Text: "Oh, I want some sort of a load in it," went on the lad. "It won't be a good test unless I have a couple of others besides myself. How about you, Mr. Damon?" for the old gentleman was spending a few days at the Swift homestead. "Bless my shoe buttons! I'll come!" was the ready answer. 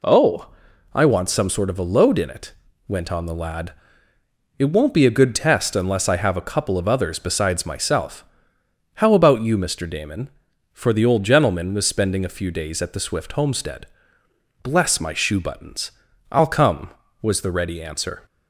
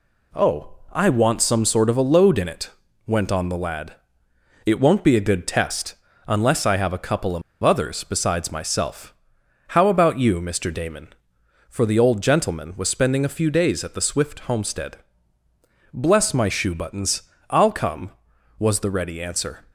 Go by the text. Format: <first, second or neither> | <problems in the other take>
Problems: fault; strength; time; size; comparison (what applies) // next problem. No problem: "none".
first | pauses between "test" and "unless"; slight; at 5.9 s; 0.32 s long // pauses between "of" and "others"; slight; at 7.4 s; 0.21 s long